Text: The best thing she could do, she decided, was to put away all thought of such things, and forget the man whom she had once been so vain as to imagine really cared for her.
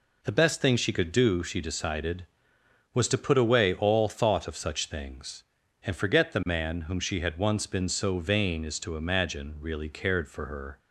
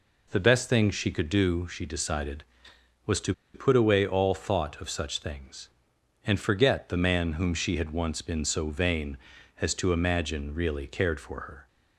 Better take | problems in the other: first | pauses between "to" and "put"; slight; at 3.3 s; 0.20 s long

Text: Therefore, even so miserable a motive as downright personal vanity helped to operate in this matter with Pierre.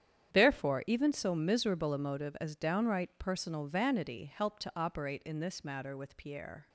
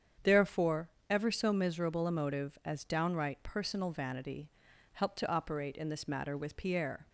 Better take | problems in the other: first | starts louder than the rest; strong; until 1.4 s; 8 dB; strong in the first // says "ever" for "even"; at 1.0 s // pauses between "vanity" and "helped"; at 4.5 s; 0.42 s long

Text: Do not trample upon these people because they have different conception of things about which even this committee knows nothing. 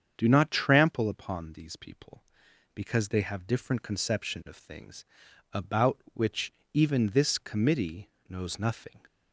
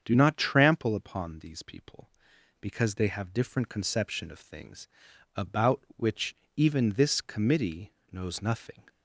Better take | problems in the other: neither | starts louder than the rest; strong; the same in both // pauses between "things" and "about"; noticeable; the same in both // pauses between "which" and "even"; slight; the same in both // pauses between "committee" and "knows"; slight; the same in both

